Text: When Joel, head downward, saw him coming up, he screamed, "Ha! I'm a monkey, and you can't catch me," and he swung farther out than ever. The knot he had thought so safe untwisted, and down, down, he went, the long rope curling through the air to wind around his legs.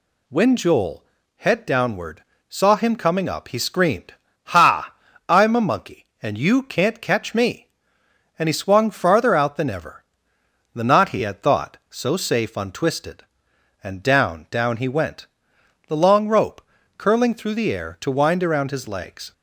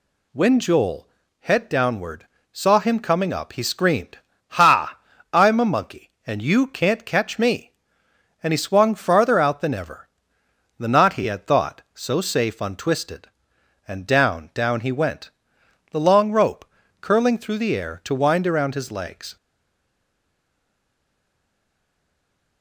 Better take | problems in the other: first | pauses between "rope" and "curling"; slight; at 16.6 s; 0.34 s long; slight in the first // stays silent after the last word; strong; from 19.3 s on; 3.3 s long

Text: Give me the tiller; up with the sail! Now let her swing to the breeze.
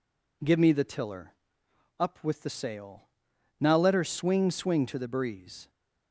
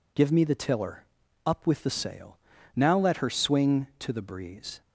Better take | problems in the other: second | says "swing" twice; at 4.5 s

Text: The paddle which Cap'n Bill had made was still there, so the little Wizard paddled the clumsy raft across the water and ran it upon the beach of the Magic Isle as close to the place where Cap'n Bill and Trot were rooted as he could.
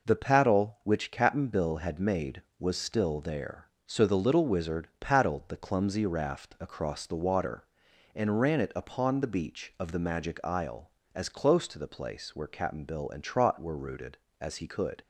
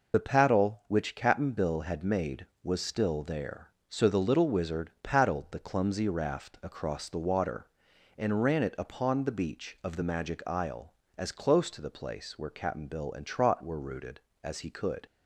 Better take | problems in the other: first | loses the start of "The"; at 0.1 s; 45 ms

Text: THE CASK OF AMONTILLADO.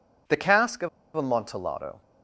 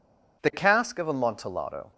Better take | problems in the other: second | pauses between "OF" and "AMONTILLADO"; slight; at 0.8 s; 0.27 s long

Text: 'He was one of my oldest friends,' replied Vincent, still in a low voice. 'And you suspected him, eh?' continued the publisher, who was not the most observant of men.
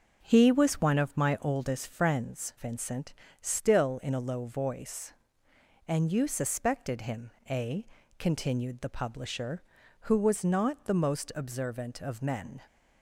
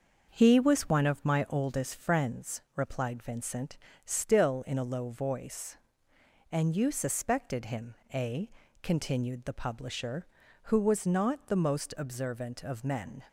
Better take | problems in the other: second | skips "replied"; at 2.5 s

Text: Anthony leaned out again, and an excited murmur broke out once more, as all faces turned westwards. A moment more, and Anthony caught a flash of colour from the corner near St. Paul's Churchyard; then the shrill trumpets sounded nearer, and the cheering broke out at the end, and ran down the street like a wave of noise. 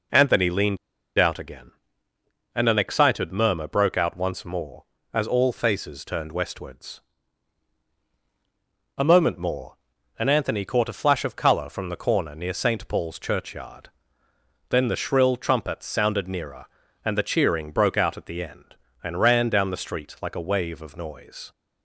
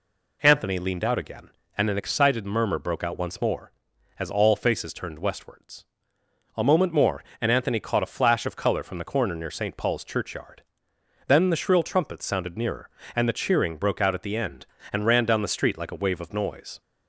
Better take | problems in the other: second | pauses between "leaned" and "out"; at 0.7 s; 0.41 s long

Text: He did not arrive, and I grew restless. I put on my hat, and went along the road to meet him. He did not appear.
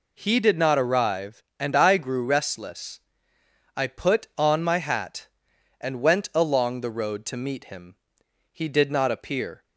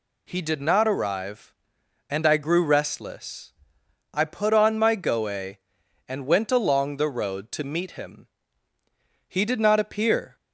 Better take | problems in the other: first | says "goe" for "hat"; at 4.9 s

